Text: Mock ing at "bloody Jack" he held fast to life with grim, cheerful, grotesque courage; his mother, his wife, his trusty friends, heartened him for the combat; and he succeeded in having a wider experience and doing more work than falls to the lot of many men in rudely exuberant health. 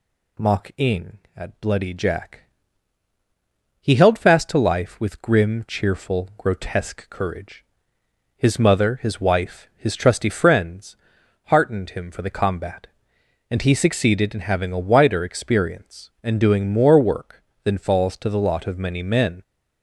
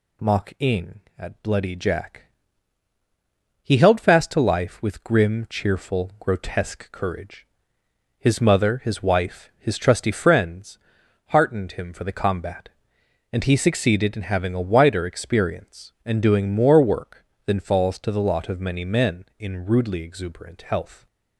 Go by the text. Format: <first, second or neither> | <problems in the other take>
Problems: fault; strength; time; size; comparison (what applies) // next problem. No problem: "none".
second | pauses between "Jack" and "he"; strong; at 2.4 s; 1.3 s long; strong in the second // stops before "in rudely exuberant health"; at 19.4 s